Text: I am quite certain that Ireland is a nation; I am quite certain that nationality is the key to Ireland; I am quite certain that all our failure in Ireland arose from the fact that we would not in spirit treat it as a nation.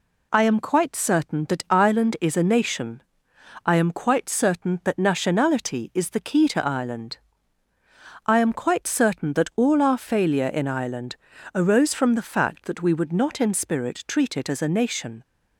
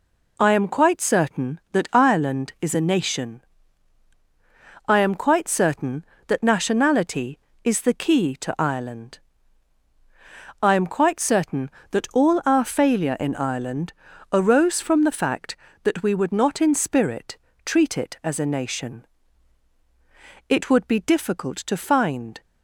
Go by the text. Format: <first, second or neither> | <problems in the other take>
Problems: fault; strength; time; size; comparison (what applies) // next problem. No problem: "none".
first | pauses between "Ireland" and "arose"; at 13.9 s; 0.40 s long; also in the first // pauses between "spirit" and "treat"; slight; at 17.3 s; 0.28 s long // goes on to say "It would be difficult to find"; strong; from 20.4 s on; 1.9 s long